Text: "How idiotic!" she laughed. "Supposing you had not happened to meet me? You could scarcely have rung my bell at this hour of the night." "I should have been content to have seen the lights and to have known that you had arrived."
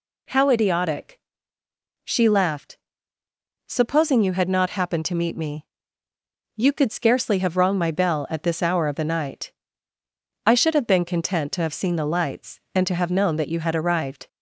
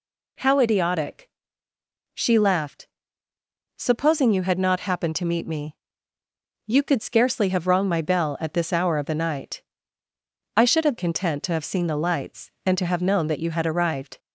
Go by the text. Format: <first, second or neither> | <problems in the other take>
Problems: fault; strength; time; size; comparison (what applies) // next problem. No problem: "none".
first | skips "been"; at 10.9 s